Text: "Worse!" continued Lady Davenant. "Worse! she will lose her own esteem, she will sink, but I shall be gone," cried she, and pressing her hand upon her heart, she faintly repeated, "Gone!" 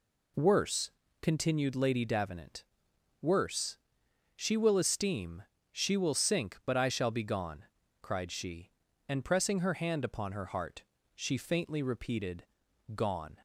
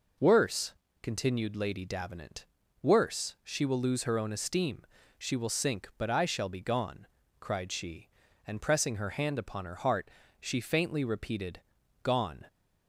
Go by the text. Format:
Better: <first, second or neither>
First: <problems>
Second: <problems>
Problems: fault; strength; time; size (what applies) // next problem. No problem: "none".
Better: second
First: skips "lose her own"; at 4.7 s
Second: none